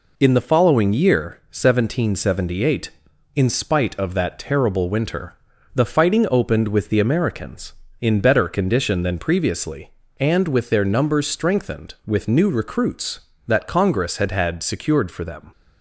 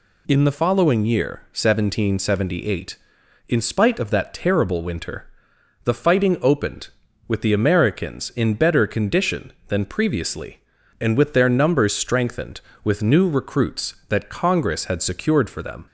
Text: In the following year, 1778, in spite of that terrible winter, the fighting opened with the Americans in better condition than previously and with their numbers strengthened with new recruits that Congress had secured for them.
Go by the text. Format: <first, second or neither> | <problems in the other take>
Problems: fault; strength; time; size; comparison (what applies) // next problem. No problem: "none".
second | says "had" twice; at 14.3 s